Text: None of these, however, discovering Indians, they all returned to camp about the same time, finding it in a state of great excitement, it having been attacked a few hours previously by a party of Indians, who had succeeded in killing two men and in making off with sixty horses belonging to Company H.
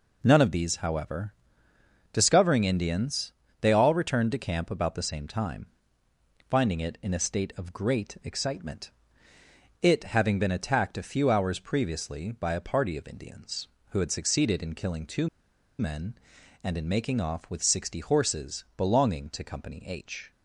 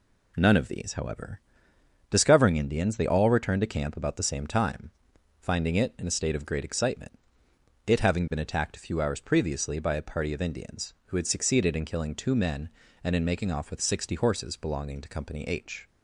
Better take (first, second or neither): second